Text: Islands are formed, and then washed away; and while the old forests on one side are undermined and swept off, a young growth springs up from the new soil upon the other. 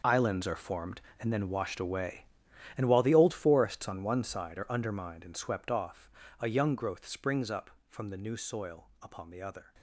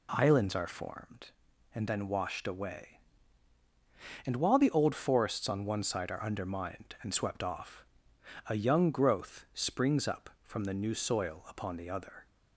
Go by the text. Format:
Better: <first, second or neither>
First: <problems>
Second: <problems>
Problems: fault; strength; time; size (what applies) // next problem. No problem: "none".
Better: second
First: gets quieter; strong; throughout; 14.5 dB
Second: none